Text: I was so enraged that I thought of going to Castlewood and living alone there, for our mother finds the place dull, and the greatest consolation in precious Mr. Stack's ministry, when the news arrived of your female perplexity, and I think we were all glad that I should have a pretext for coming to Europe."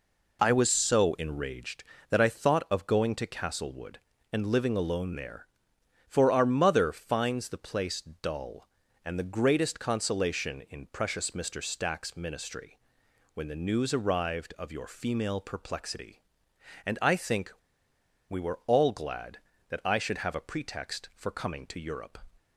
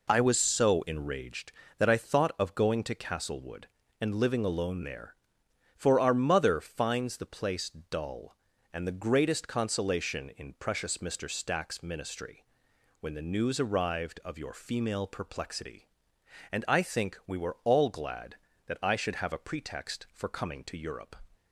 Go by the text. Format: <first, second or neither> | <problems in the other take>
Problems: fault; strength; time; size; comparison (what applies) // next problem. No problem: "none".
second | pauses between "place" and "dull"; slight; at 8.0 s; 0.20 s long; slight in the second // pauses between "think" and "we"; noticeable; at 17.5 s; 0.76 s long